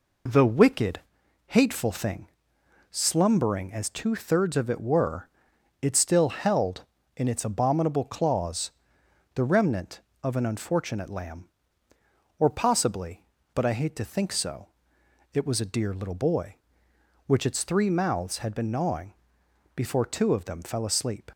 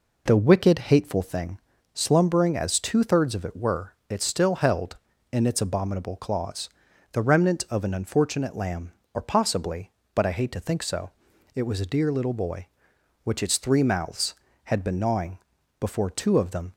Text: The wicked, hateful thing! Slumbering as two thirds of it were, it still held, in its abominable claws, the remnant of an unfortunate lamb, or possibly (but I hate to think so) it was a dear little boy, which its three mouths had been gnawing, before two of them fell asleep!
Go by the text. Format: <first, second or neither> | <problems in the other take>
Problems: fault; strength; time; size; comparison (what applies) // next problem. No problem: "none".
first | stops before "fell asleep"; at 16.7 s